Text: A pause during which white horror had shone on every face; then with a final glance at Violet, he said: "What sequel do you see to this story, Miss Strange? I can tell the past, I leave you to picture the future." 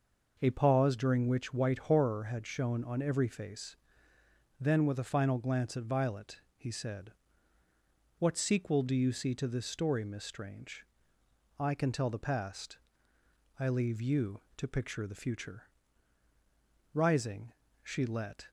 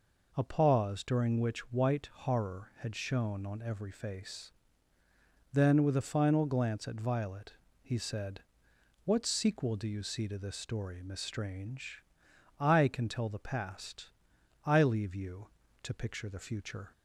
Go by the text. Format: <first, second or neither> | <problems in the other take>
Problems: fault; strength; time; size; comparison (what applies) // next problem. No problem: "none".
second | goes on to say "Rising she let"; from 16.9 s on; 1.5 s long